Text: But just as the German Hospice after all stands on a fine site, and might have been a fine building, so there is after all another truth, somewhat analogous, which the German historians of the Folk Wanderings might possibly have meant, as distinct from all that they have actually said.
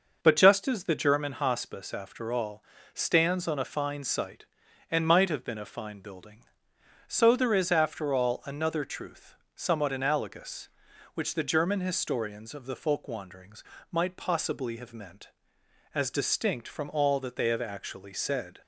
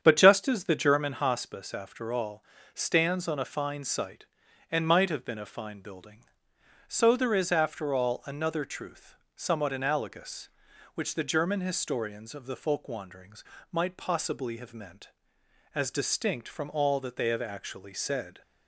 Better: first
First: pauses between "all" and "stands"; slight; at 2.6 s; 0.30 s long // pauses between "Wanderings" and "might"; slight; at 13.6 s; 0.28 s long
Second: starts louder than the rest; strong; until 1.4 s; 8 dB // pauses between "all" and "stands"; slight; at 2.4 s; 0.30 s long // pauses between "Wanderings" and "might"; slight; at 13.4 s; 0.28 s long

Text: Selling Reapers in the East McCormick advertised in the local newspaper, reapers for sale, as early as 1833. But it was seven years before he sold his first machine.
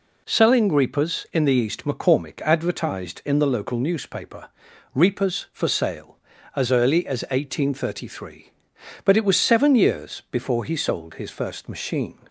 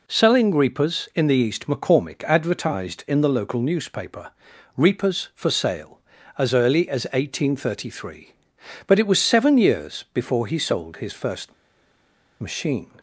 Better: first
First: none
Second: pauses between "first" and "machine"; noticeable; at 11.5 s; 0.89 s long

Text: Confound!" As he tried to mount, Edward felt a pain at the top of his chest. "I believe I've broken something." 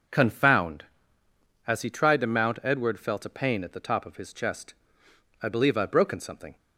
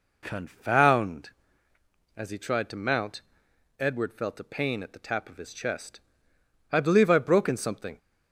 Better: first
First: none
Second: says "tap" for "top"; at 5.0 s

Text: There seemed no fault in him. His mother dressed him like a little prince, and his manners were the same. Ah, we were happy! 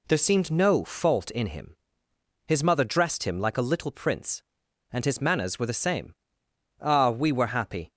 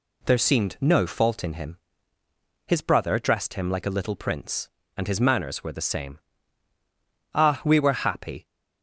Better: first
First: none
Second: says "brother" for "mother"; at 2.8 s

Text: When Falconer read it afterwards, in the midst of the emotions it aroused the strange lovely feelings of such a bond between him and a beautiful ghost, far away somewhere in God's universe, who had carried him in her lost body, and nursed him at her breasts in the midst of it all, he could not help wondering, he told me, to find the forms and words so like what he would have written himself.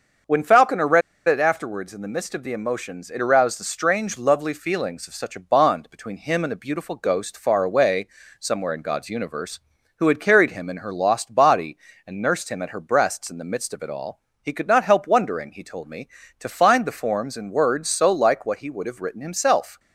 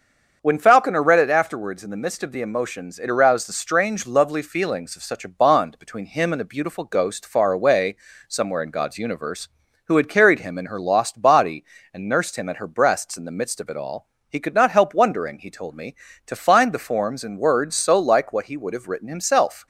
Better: second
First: starts louder than the rest; until 1.5 s; 6.5 dB // pauses between "read" and "it"; slight; at 1.0 s; 0.26 s long // pauses between "away" and "somewhere"; slight; at 8.0 s; 0.32 s long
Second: starts louder than the rest; until 1.4 s; 7 dB // pauses between "away" and "somewhere"; slight; at 7.9 s; 0.32 s long

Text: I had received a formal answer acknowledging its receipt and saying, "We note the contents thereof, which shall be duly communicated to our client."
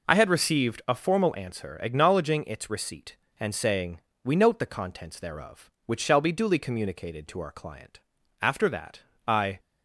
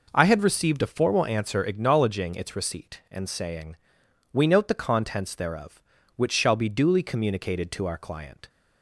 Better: second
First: goes on to say "After that I"; noticeable; from 8.4 s on; 1.1 s long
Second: none

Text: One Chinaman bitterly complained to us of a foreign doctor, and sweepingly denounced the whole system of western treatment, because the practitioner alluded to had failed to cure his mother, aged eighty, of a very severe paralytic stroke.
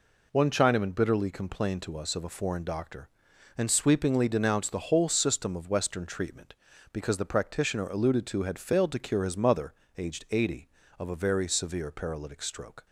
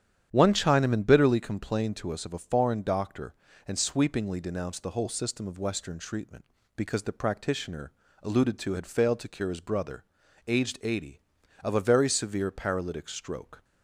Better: first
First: none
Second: starts louder than the rest; strong; until 1.3 s; 9.5 dB // pauses between "practitioner" and "alluded"; slight; at 7.8 s; 0.32 s long // says "brother" for "mother"; at 9.5 s

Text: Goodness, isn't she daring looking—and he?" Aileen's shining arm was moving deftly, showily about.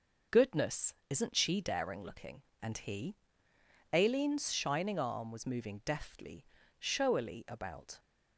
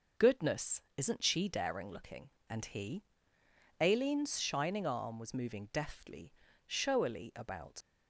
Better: first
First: none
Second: leaves "about" unfinished; at 7.8 s; 55 ms

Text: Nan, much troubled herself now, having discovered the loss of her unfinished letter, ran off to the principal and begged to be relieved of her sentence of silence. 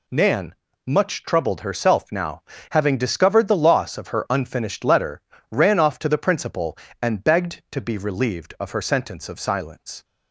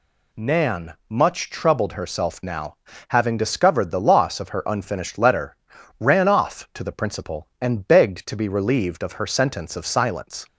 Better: neither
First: none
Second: none

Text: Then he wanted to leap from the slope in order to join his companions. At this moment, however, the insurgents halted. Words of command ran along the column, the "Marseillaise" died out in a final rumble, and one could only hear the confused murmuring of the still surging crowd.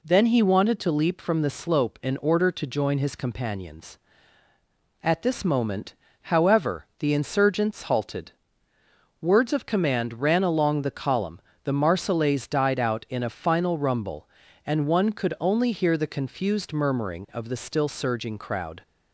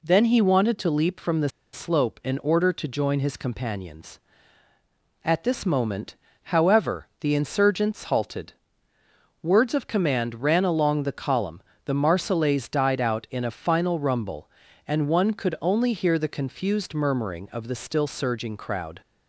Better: first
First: none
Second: pauses between "the" and "slope"; slight; at 1.4 s; 0.24 s long

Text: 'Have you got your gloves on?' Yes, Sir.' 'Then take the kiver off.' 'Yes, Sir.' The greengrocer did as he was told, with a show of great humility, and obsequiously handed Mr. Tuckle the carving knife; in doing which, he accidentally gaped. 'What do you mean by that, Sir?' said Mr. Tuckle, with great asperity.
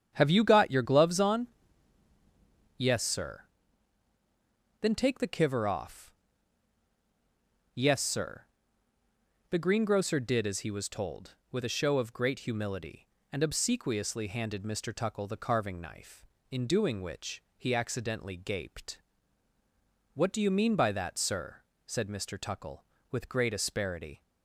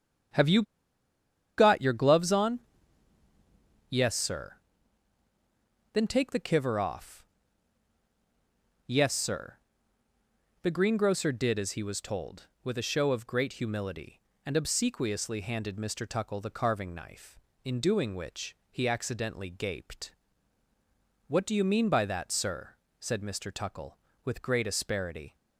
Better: first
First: starts louder than the rest; strong; until 1.1 s; 8.5 dB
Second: starts louder than the rest; strong; until 2.2 s; 8.5 dB // pauses between "you" and "got"; noticeable; at 0.6 s; 0.95 s long

